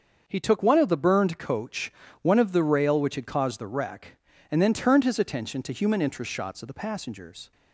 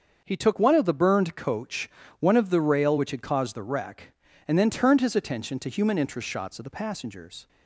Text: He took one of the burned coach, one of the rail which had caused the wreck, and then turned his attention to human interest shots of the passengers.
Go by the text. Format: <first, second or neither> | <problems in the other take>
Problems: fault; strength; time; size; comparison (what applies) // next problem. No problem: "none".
neither | starts louder than the rest; the same in both